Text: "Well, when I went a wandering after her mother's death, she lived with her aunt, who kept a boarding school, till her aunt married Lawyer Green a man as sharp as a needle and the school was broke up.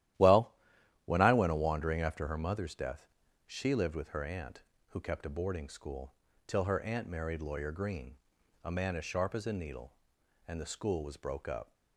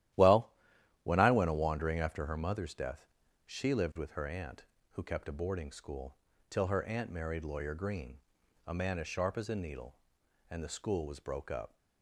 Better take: neither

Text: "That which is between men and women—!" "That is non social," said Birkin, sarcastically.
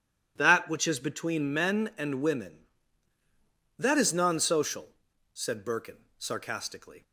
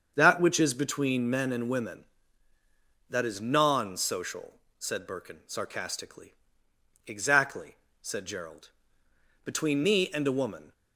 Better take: first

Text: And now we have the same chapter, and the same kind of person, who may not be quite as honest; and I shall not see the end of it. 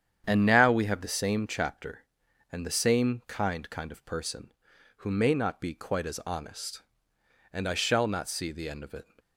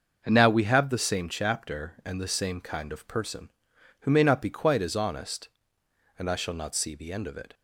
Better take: second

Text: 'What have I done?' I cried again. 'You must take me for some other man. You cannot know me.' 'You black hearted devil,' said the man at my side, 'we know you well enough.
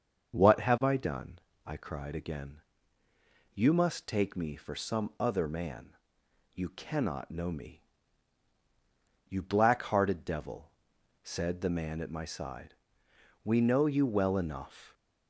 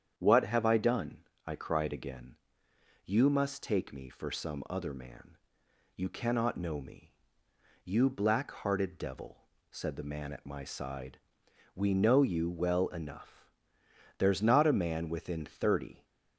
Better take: first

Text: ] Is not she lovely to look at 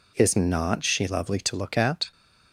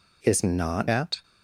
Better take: first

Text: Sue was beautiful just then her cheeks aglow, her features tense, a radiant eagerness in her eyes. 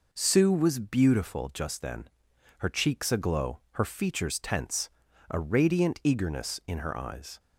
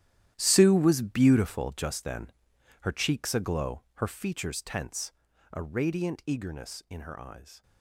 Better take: first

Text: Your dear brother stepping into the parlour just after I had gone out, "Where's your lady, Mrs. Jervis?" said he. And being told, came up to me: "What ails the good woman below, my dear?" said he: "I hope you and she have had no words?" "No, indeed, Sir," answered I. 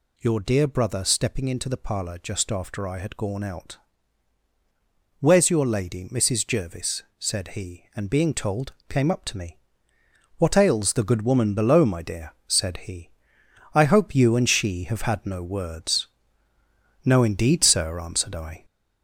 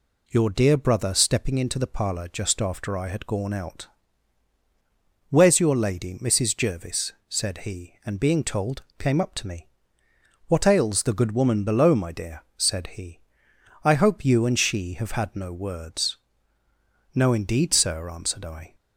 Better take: second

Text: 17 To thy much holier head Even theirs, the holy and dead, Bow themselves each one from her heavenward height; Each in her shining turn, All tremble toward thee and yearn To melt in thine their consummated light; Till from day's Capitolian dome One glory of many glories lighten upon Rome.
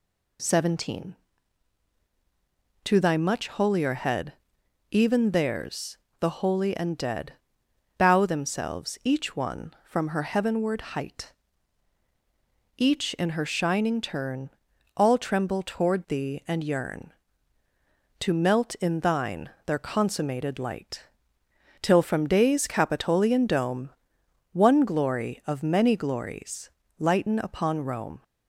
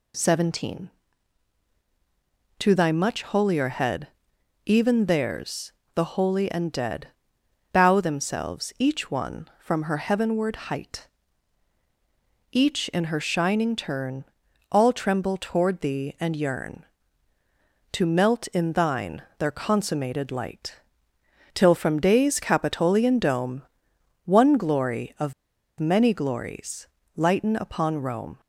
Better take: first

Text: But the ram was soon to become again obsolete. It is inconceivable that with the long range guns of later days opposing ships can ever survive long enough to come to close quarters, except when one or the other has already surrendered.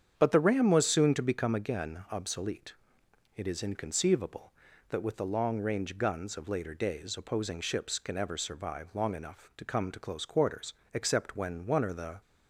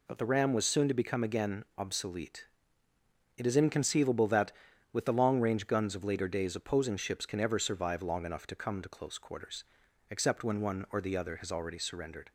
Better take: second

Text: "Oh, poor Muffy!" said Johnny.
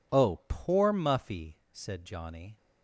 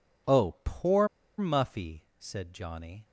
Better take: first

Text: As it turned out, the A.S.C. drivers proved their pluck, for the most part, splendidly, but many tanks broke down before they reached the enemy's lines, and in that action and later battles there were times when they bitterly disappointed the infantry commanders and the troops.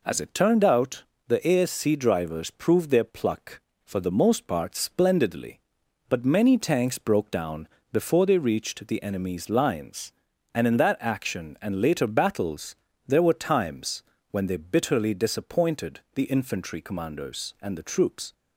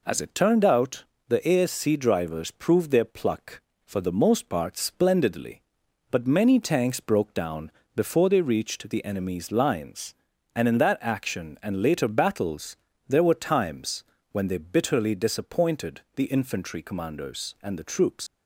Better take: first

